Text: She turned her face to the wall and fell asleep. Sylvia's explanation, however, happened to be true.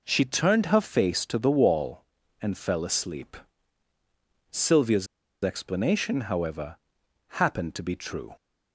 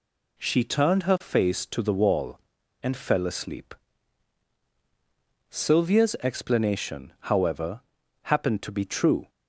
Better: second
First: pauses between "Sylvia's" and "explanation"; at 5.0 s; 0.38 s long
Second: none

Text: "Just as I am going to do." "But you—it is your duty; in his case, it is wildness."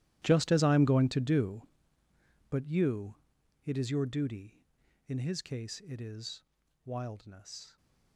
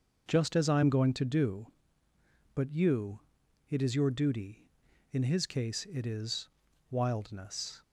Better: second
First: gets quieter; strong; throughout; 19 dB // pauses between "is" and "wildness"; at 6.4 s; 0.42 s long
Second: pauses between "is" and "wildness"; at 6.4 s; 0.42 s long

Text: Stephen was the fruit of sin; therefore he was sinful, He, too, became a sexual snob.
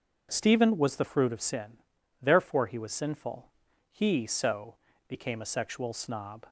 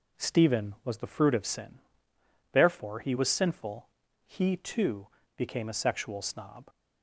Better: second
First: says "so" for "too"; at 4.2 s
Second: none

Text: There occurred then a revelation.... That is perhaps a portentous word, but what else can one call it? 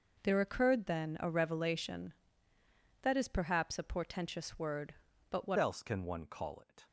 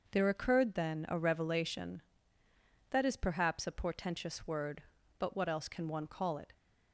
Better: second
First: changes voice at "else"; from 5.5 s on; 1.3 s long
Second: none

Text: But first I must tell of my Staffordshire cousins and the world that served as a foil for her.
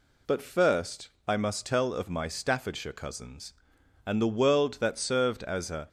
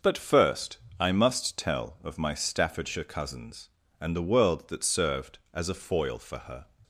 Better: second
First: pauses between "first" and "I"; slight; at 1.1 s; 0.18 s long // stops before "foil for her"; at 5.8 s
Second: pauses between "first" and "I"; slight; at 0.7 s; 0.22 s long

